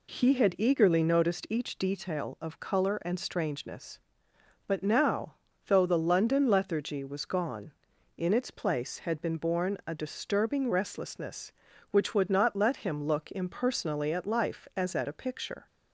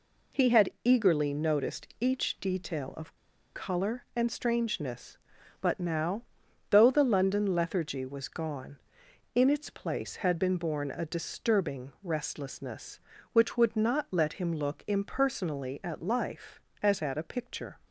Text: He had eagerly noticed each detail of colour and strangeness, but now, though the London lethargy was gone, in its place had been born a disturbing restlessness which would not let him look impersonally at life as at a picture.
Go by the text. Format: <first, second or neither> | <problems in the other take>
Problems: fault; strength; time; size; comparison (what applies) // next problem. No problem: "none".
first | pauses between "of" and "colour"; at 3.1 s; 0.40 s long